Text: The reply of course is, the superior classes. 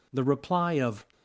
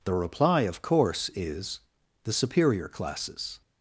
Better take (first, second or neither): second